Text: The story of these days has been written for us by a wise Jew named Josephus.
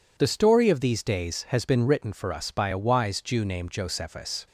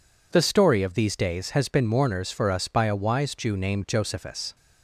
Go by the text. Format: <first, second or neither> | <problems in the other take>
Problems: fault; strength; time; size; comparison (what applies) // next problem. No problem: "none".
first | says "mourners" for "written"; at 1.8 s